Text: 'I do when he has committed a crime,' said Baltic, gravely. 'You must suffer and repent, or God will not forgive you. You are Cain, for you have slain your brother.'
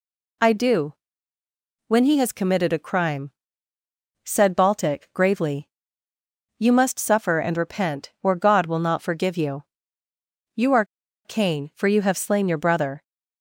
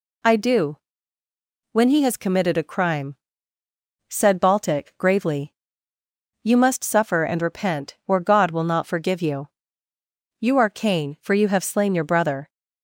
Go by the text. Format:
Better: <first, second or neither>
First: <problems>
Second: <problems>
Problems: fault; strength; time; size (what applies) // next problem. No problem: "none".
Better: second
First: pauses between "do" and "when"; noticeable; at 0.9 s; 0.92 s long // pauses between "are" and "Cain"; at 10.8 s; 0.40 s long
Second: pauses between "do" and "when"; noticeable; at 0.7 s; 0.93 s long